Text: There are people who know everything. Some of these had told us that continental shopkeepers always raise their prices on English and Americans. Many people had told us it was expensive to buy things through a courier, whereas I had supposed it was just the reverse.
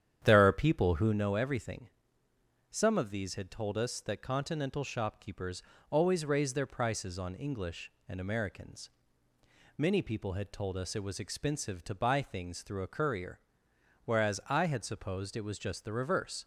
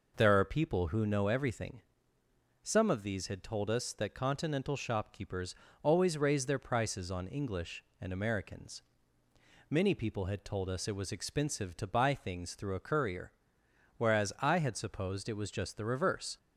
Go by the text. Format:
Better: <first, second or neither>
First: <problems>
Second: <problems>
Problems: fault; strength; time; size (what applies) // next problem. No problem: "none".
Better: second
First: starts louder than the rest; strong; until 1.2 s; 9.5 dB // pauses between "shopkeepers" and "always"; slight; at 5.6 s; 0.30 s long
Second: pauses between "shopkeepers" and "always"; slight; at 5.5 s; 0.30 s long